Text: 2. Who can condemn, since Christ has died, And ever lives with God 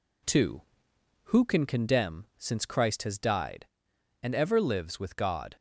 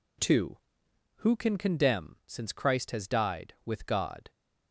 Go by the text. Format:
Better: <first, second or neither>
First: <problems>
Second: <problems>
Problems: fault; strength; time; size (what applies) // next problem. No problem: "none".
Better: first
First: none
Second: skips "And ever lives"; at 3.5 s